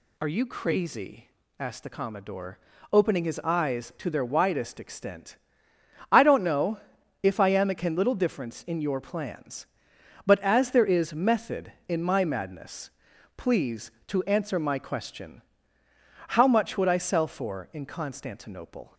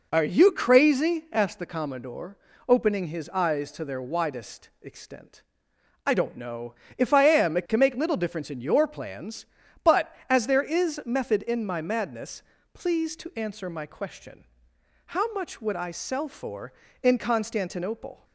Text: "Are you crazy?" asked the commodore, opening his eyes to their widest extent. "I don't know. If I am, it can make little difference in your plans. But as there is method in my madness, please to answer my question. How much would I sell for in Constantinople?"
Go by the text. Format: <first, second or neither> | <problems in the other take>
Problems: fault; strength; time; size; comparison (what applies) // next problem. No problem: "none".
second | skips "make"; at 7.9 s